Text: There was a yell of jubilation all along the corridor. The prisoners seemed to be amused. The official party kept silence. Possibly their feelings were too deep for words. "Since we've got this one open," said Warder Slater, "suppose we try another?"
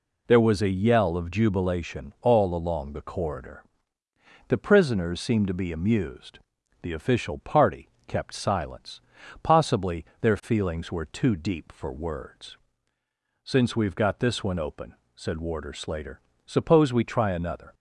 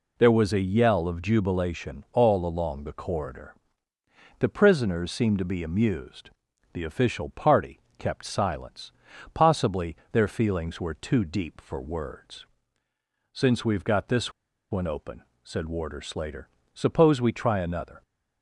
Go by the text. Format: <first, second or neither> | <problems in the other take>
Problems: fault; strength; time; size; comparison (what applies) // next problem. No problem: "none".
first | pauses between "party" and "kept"; slight; at 7.8 s; 0.18 s long; slight in the first // pauses between "Possibly" and "their"; slight; at 9.9 s; 0.18 s long; slight in the first // pauses between "this" and "one"; at 14.3 s; 0.39 s long